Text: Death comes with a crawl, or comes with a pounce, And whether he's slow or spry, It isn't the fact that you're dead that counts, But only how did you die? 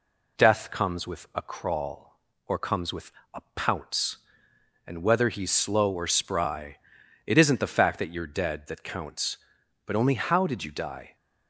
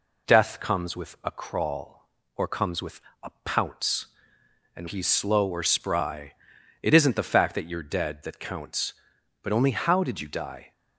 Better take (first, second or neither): first